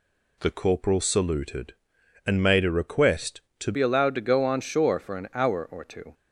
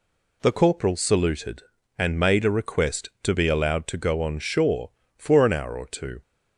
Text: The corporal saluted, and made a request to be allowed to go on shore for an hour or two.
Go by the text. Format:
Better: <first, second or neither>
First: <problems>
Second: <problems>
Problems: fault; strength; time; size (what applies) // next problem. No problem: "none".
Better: second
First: changes voice at "be"; from 3.7 s on; 2.4 s long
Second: none